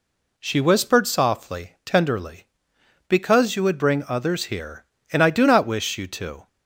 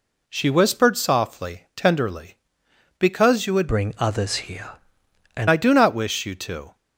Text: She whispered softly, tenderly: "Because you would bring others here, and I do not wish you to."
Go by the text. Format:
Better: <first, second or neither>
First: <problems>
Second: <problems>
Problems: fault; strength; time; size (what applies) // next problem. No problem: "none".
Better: first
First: none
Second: changes voice from "bring" to "and"; from 3.6 to 5.4 s; 1.8 s long